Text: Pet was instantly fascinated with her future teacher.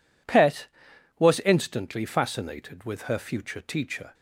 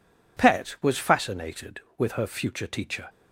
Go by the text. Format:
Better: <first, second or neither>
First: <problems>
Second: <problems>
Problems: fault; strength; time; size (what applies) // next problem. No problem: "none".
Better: first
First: none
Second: skips "instantly"; at 0.9 s